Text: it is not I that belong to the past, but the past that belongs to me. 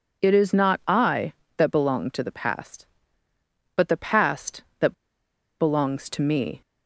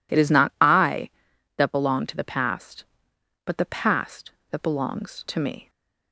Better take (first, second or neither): second